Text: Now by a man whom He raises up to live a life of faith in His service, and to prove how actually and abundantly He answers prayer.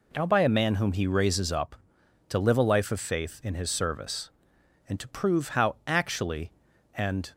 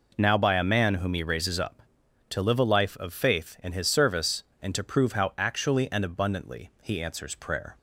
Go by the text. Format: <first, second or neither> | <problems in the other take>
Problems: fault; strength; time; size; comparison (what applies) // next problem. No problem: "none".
second | stops before "abundantly He answers prayer"; at 7.3 s